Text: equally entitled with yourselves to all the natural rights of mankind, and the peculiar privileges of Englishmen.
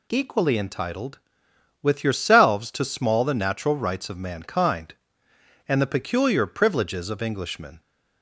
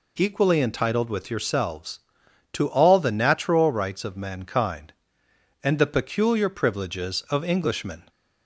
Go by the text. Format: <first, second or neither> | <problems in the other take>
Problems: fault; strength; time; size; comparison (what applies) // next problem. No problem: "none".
second | says "small" for "all"; at 2.8 s